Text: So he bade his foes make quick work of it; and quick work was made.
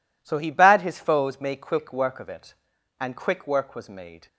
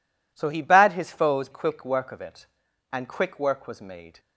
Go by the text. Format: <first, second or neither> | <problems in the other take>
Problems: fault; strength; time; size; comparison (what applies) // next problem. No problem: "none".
first | skips "make"; at 1.5 s